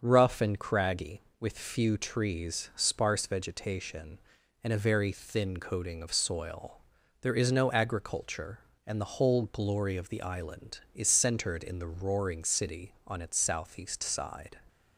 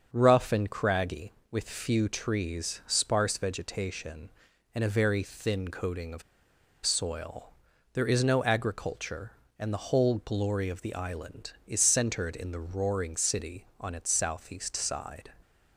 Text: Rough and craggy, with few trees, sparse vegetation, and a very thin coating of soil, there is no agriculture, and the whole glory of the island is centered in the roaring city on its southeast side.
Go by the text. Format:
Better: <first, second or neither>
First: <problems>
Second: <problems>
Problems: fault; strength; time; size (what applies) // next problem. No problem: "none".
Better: first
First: starts louder than the rest; until 1.0 s; 6.5 dB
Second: starts louder than the rest; until 1.1 s; 6.5 dB // pauses between "of" and "soil"; noticeable; at 6.2 s; 0.63 s long